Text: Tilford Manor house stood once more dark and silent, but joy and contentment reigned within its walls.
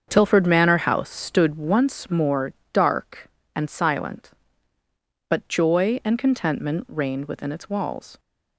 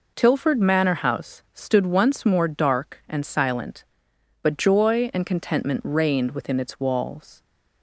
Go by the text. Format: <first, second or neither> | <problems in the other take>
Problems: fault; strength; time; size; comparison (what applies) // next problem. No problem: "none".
second | starts louder than the rest; strong; until 1.8 s; 7 dB // pauses between "more" and "dark"; slight; at 2.5 s; 0.20 s long